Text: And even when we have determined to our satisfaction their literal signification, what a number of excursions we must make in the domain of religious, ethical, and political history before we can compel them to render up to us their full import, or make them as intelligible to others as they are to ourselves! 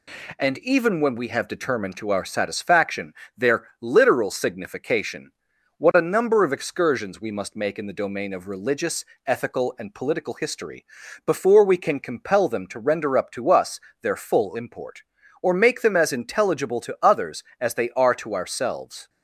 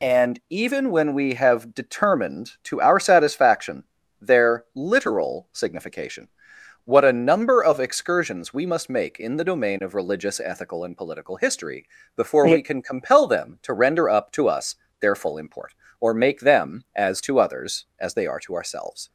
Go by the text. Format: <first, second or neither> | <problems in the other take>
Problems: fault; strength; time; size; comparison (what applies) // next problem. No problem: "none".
first | pauses between "satisfaction" and "their"; slight; at 3.8 s; 0.36 s long; slight in the first // pauses between "history" and "before"; slight; at 11.8 s; 0.30 s long; also in the first // pauses between "us" and "their"; slight; at 14.7 s; 0.24 s long; slight in the first // skips "intelligible"; at 17.2 s